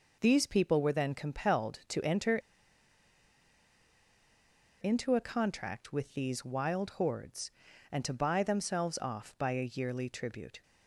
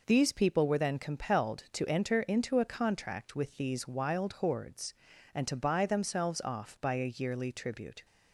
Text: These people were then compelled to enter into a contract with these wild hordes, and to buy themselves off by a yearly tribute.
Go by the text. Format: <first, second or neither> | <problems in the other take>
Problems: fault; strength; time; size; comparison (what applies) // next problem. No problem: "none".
second | pauses between "enter" and "into"; strong; at 2.3 s; 2.4 s long